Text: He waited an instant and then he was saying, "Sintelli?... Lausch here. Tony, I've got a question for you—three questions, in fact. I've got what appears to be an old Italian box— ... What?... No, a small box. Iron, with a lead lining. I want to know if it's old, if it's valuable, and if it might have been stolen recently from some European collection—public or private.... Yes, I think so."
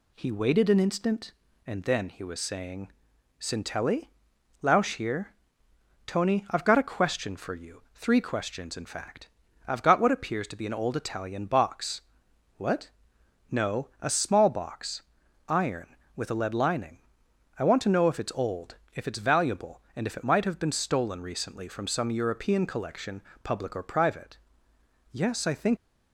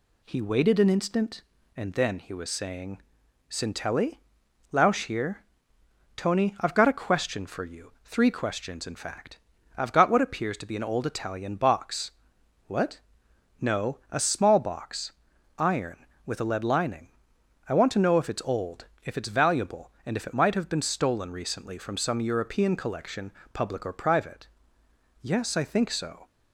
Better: second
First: stops before "so"; at 25.7 s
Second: none

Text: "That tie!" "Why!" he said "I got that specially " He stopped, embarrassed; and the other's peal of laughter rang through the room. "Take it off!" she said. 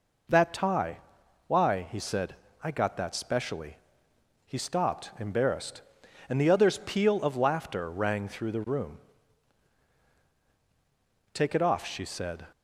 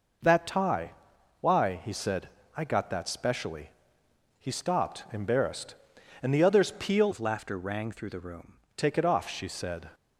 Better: first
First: pauses between "said" and "I"; slight; at 2.3 s; 0.28 s long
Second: pauses between "said" and "I"; slight; at 2.2 s; 0.28 s long // changes voice from "of" to "room"; from 7.1 to 8.5 s; 1.4 s long

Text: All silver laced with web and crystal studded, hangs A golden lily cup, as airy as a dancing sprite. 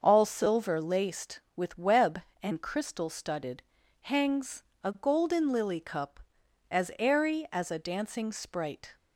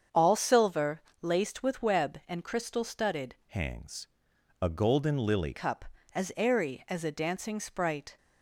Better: first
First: starts louder than the rest; until 1.0 s; 6.5 dB // pauses between "hangs" and "A"; slight; at 4.6 s; 0.18 s long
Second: starts louder than the rest; strong; until 1.3 s; 7.5 dB // pauses between "silver" and "laced"; slight; at 1.0 s; 0.20 s long // changes voice from "hangs" to "lily"; from 3.4 to 5.5 s; 2.1 s long // pauses between "hangs" and "A"; noticeable; at 4.0 s; 0.54 s long

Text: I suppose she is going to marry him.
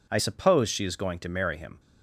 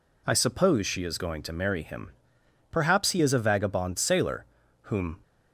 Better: first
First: none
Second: goes on to say "Perhaps he is a vagabond sailor whom"; strong; from 2.7 s on; 2.4 s long

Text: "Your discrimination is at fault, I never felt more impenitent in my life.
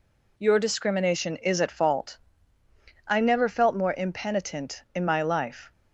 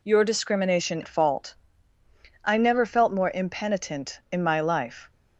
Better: first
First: none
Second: skips "is"; at 1.0 s

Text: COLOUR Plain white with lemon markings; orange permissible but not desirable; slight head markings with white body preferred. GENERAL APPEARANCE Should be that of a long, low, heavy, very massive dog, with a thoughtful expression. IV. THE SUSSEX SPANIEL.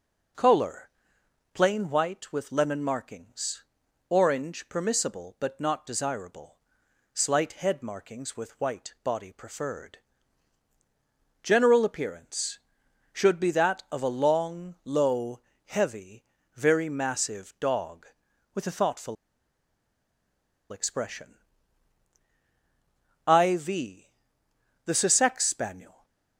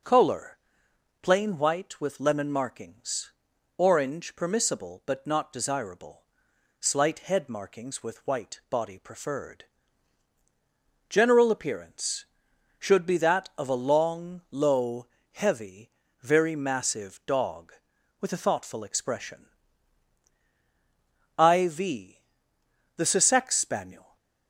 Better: second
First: pauses between "COLOUR" and "Plain"; noticeable; at 0.8 s; 0.64 s long // pauses between "thoughtful" and "expression"; strong; at 19.1 s; 1.5 s long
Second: pauses between "COLOUR" and "Plain"; noticeable; at 0.5 s; 0.64 s long

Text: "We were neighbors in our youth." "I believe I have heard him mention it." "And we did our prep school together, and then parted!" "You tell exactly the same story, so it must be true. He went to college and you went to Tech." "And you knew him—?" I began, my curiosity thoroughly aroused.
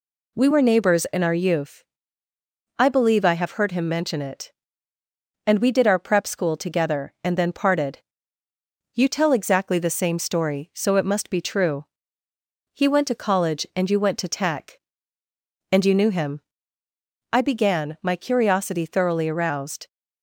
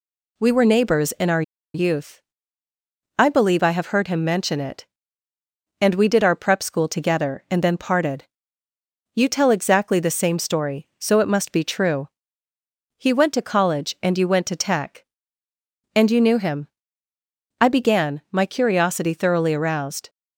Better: first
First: none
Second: pauses between "our" and "youth"; slight; at 1.4 s; 0.32 s long

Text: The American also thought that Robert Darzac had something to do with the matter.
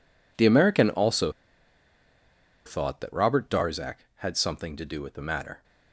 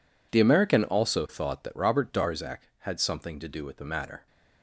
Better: second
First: pauses between "also" and "thought"; strong; at 1.3 s; 1.3 s long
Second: none

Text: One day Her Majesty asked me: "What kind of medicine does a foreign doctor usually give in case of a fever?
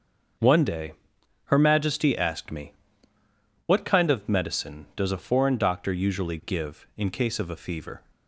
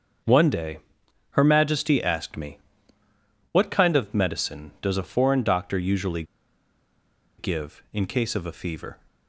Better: first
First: starts louder than the rest; until 1.9 s; 6.5 dB // pauses between "day" and "Her"; noticeable; at 0.9 s; 0.54 s long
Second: starts louder than the rest; until 1.7 s; 6.5 dB // pauses between "day" and "Her"; noticeable; at 0.7 s; 0.54 s long // pauses between "usually" and "give"; at 6.2 s; 1.1 s long

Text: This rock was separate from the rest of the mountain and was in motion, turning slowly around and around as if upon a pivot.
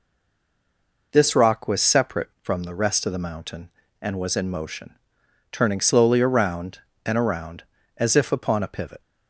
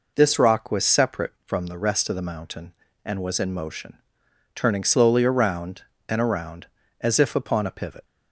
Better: second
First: stays silent before the first word; until 1.1 s; 1.1 s long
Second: none

